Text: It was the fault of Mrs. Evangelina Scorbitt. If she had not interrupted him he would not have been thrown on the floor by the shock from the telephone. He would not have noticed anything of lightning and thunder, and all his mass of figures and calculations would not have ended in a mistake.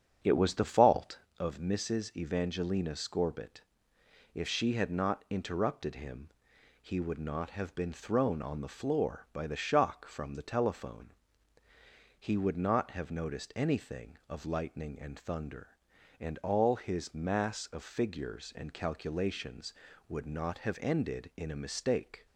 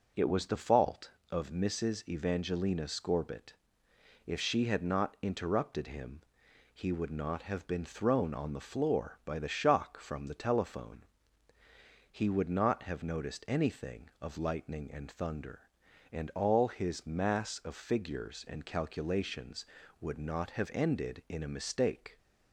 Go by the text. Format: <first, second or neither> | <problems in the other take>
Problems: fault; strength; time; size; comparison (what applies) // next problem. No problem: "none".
second | starts louder than the rest; strong; until 1.4 s; 7.5 dB // pauses between "him" and "he"; noticeable; at 6.2 s; 0.52 s long; noticeable in the second